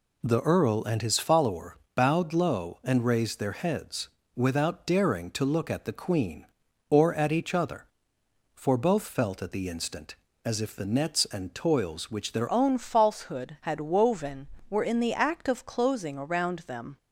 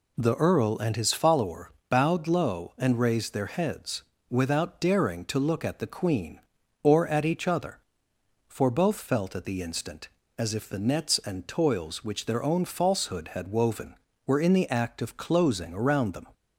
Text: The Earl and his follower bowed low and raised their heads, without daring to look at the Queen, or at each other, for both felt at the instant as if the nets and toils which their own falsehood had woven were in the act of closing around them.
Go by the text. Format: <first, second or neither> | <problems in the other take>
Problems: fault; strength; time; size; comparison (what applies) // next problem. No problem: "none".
second | pauses between "follower" and "bowed"; slight; at 1.7 s; 0.18 s long; slight in the second // changes voice at "own"; from 12.5 s on; 4.4 s long